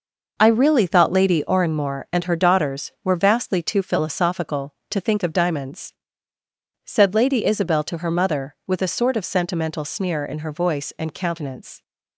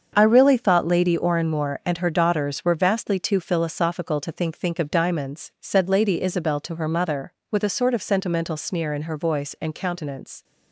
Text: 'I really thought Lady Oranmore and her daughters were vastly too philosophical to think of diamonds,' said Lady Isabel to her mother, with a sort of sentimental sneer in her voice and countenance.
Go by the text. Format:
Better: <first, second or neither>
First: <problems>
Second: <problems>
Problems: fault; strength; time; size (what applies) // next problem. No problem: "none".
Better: first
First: none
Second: starts louder than the rest; until 1.1 s; 7 dB // says "think" twice; at 4.5 s